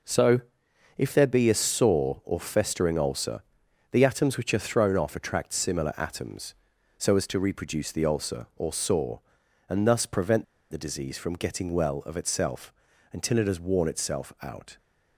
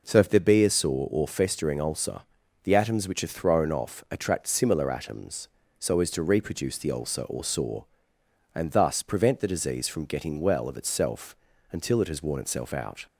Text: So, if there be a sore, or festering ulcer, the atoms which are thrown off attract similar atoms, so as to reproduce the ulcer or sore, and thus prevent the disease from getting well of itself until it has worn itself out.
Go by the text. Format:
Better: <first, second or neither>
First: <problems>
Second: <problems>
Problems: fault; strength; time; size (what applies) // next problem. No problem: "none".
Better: second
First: pauses between "prevent" and "the"; slight; at 10.4 s; 0.26 s long // pauses between "itself" and "until"; at 12.7 s; 0.40 s long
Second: pauses between "itself" and "until"; slight; at 11.3 s; 0.34 s long